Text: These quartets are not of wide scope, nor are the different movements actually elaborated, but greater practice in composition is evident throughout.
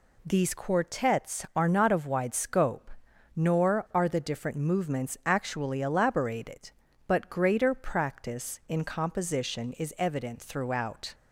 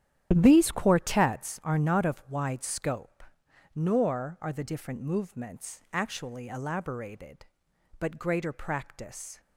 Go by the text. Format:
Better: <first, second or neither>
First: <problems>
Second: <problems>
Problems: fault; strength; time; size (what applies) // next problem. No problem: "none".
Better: first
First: none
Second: starts louder than the rest; strong; until 1.3 s; 10.5 dB // stops before "in composition is evident throughout"; at 9.4 s